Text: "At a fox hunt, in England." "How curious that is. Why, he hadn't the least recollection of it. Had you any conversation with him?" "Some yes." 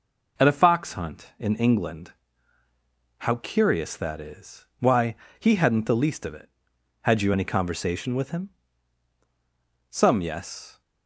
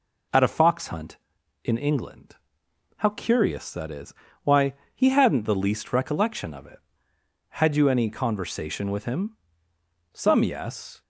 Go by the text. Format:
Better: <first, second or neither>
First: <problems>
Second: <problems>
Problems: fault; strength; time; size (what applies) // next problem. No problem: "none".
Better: second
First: skips "recollection"; at 6.2 s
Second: none